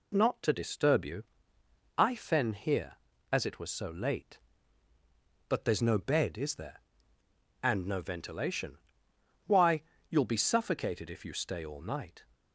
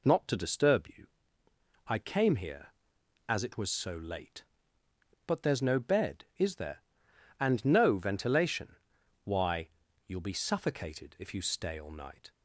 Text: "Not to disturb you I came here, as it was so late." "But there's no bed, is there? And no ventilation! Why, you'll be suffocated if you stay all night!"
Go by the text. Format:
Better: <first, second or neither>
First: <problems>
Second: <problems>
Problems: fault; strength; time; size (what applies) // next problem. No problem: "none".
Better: second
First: pauses between "you" and "I"; noticeable; at 1.2 s; 0.74 s long // says "fen" for "came"; at 2.1 s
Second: pauses between "you" and "I"; noticeable; at 1.0 s; 0.80 s long